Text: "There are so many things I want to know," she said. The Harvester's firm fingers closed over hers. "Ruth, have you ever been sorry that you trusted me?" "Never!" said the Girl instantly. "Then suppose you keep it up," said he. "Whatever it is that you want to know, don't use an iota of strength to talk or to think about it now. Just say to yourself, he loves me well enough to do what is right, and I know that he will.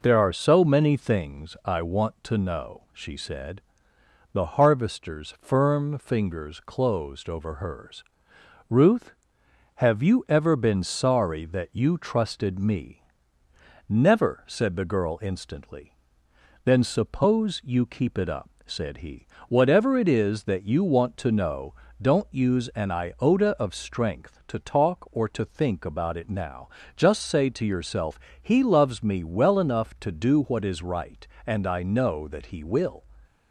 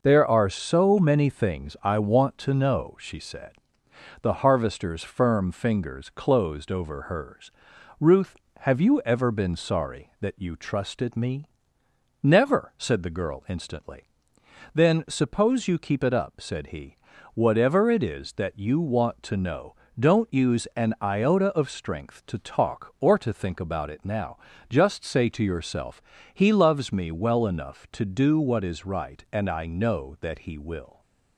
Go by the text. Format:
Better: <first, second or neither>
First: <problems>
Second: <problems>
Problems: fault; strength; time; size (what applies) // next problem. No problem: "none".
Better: neither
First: none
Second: none